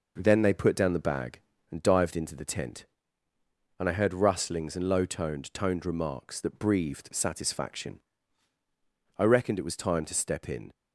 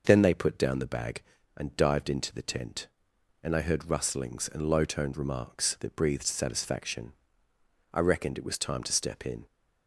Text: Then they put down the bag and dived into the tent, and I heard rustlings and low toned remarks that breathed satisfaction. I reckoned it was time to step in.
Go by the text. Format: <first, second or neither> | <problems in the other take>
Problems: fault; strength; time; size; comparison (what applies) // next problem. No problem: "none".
second | says "toned" twice; at 5.5 s